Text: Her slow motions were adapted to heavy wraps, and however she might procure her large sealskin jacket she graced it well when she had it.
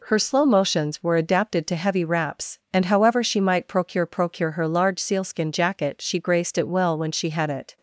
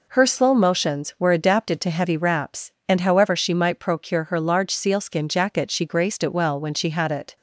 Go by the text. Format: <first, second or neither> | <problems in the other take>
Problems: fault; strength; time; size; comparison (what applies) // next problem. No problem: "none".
second | says "procure" twice; at 4.0 s